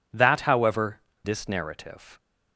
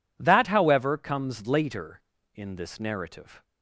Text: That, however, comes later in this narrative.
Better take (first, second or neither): second